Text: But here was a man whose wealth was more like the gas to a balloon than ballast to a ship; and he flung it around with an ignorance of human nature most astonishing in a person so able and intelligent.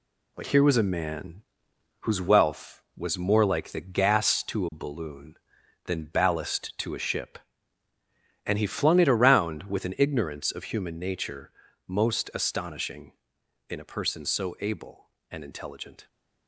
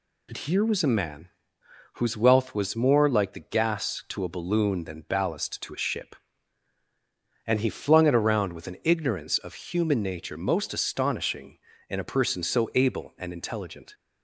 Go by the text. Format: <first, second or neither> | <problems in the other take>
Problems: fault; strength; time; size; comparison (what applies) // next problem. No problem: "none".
second | gets quieter; noticeable; throughout; 5.5 dB // pauses between "man" and "whose"; noticeable; at 1.4 s; 0.58 s long; noticeable in the second // pauses between "nature" and "most"; slight; at 11.5 s; 0.36 s long